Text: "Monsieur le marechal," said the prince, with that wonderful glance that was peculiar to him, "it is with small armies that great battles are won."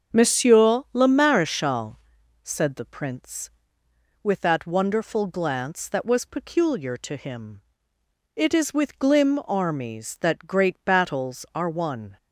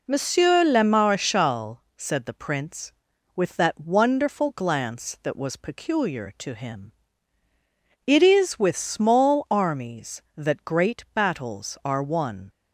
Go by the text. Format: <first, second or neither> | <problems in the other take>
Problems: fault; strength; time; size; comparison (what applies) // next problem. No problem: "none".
second | starts louder than the rest; until 1.2 s; 7 dB // says "glim" for "small"; at 8.9 s